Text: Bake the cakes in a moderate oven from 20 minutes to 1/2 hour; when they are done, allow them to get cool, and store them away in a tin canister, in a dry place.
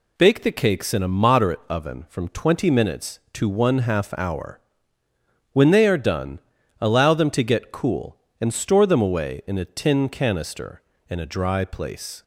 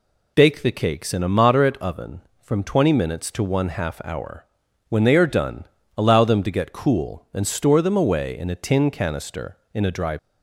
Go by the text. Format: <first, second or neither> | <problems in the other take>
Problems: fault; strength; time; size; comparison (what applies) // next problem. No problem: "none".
first | stops before "place"; at 10.1 s